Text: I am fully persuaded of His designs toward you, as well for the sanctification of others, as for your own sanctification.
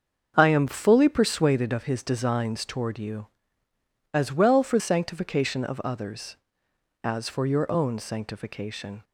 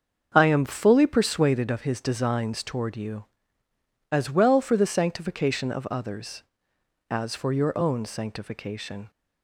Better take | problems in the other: second | starts louder than the rest; until 1.3 s; 7 dB; also in the second // skips "the"; at 4.7 s

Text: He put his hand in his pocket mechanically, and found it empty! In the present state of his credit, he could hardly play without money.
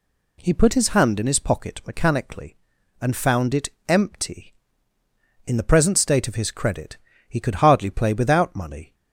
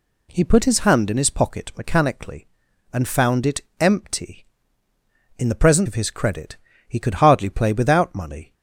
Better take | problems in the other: first | pauses between "it" and "empty"; slight; at 3.6 s; 0.18 s long; slight in the first // skips "state"; at 5.8 s

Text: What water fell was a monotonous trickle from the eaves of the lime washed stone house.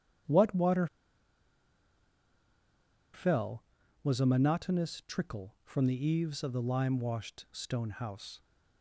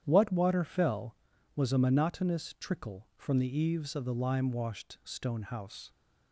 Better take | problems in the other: second | starts louder than the rest; strong; until 3.5 s; 9.5 dB; strong in the second // pauses between "water" and "fell"; strong; at 0.8 s; 2.2 s long

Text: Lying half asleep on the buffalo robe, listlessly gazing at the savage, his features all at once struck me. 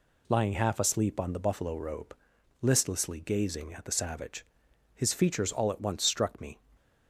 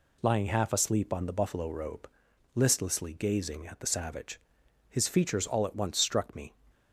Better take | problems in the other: neither | none

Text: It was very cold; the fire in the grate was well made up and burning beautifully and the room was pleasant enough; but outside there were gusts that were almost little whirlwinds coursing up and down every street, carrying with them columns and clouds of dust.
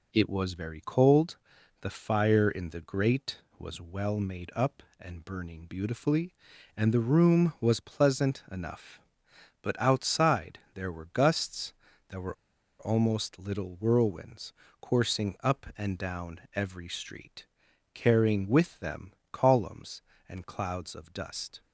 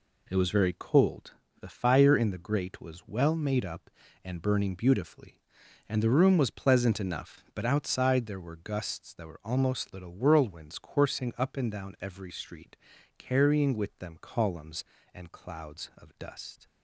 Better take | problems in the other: second | pauses between "outside" and "there"; slight; at 10.5 s; 0.16 s long // pauses between "were" and "almost"; at 12.3 s; 0.45 s long // pauses between "whirlwinds" and "coursing"; slight; at 14.5 s; 0.26 s long // pauses between "them" and "columns"; slight; at 19.1 s; 0.20 s long

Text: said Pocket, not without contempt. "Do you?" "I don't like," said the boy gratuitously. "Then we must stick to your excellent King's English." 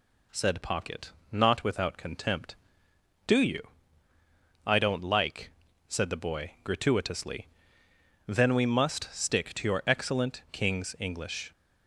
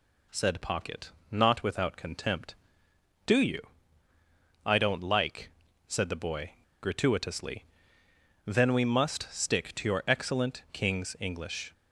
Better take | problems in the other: first | pauses between "boy" and "gratuitously"; slight; at 6.5 s; 0.31 s long

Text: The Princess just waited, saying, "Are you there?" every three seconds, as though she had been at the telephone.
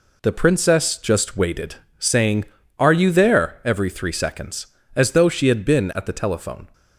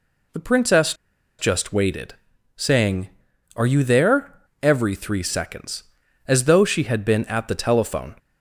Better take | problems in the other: first | pauses between "Princess" and "just"; at 0.9 s; 0.45 s long

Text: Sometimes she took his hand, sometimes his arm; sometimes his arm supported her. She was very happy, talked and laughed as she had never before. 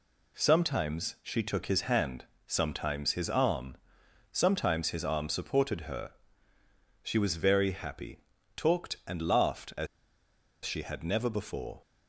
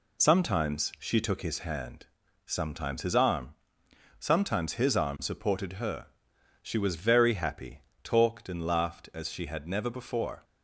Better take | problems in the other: second | pauses between "as" and "she"; noticeable; at 9.8 s; 0.78 s long

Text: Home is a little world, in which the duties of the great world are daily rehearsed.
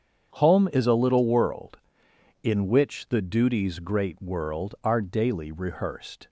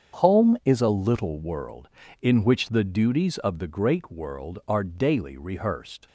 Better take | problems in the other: second | starts louder than the rest; strong; until 1.3 s; 8 dB; strong in the second // skips "of the"; at 3.7 s

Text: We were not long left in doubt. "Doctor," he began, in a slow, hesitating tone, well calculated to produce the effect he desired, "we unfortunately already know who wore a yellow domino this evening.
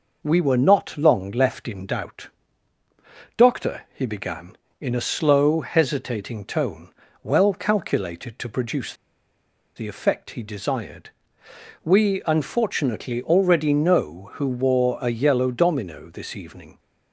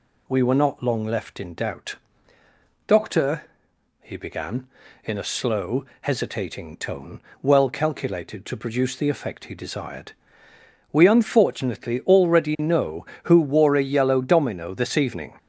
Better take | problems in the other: second | pauses between "produce" and "the"; noticeable; at 8.9 s; 0.82 s long

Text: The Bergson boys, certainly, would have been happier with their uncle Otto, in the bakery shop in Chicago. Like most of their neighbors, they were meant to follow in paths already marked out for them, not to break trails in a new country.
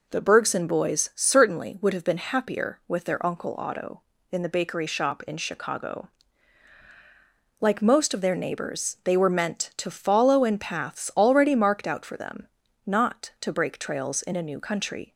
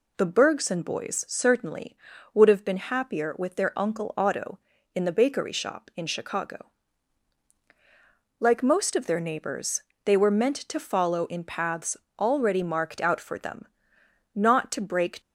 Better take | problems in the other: first | pauses between "paths" and "already"; slight; at 11.9 s; 0.20 s long // stops before "trails in a new country"; at 15.2 s

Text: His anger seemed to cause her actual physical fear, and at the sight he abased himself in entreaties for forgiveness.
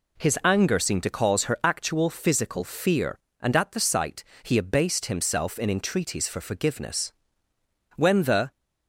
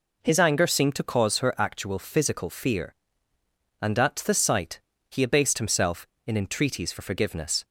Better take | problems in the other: second | pauses between "sight" and "he"; slight; at 4.2 s; 0.18 s long; slight in the second // goes on to say "When the"; from 7.9 s on; 0.60 s long

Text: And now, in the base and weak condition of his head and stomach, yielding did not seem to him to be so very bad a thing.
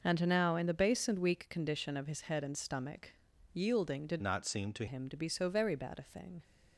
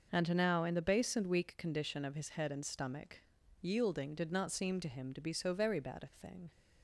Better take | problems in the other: second | changes voice from "not" to "to"; from 4.2 to 4.8 s; 0.6 s long

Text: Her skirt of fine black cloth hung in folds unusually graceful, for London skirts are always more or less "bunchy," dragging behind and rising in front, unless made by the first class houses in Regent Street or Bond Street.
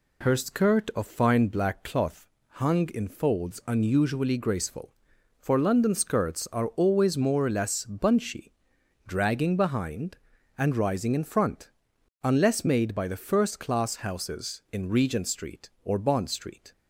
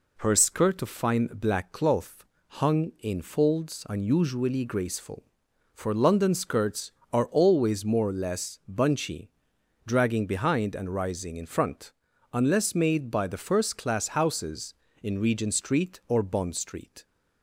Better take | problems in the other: neither | pauses between "cloth" and "hung"; slight; the same in both

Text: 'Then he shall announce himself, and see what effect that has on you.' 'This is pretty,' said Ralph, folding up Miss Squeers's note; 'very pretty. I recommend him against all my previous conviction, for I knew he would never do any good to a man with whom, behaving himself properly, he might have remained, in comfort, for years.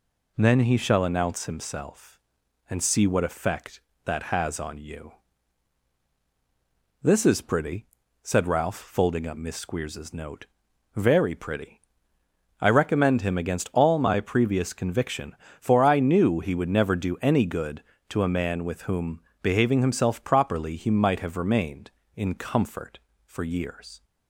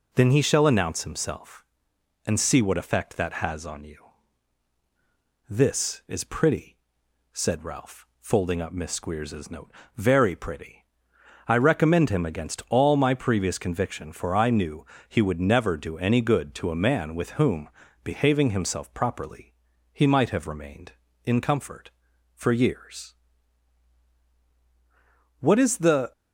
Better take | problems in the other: first | pauses between "knew" and "he"; slight; at 14.8 s; 0.22 s long // goes on to say "What is the"; noticeable; from 25.3 s on; 0.72 s long

